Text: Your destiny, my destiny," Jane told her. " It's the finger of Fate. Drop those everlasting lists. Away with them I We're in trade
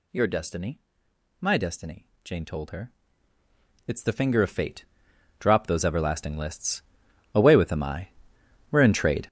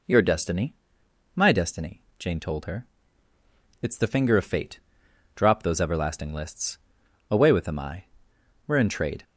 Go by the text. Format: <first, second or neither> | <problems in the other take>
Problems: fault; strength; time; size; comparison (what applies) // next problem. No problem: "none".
second | gets louder; strong; throughout; 17 dB // pauses between "I" and "We're"; noticeable; at 8.0 s; 0.62 s long; noticeable in the second